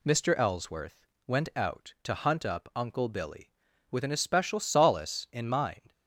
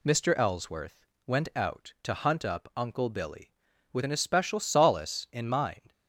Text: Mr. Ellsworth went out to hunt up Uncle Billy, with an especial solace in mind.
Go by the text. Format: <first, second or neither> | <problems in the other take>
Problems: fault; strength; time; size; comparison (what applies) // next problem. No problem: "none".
neither | pauses between "Ellsworth" and "went"; slight; the same in both